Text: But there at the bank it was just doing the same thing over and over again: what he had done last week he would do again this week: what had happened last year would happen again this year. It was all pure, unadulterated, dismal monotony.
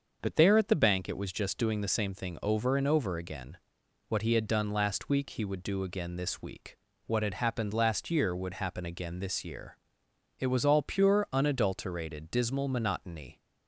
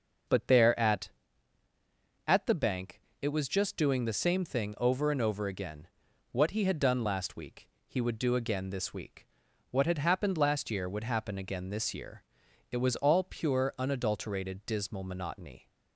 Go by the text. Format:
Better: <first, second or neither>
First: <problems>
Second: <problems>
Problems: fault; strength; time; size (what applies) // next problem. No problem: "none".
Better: first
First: starts louder than the rest; until 1.2 s; 6.5 dB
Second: starts louder than the rest; noticeable; until 2.4 s; 6 dB // says "at" twice; at 2.2 s // pauses between "bank" and "it"; slight; at 3.0 s; 0.20 s long // pauses between "week" and "he"; slight; at 7.6 s; 0.20 s long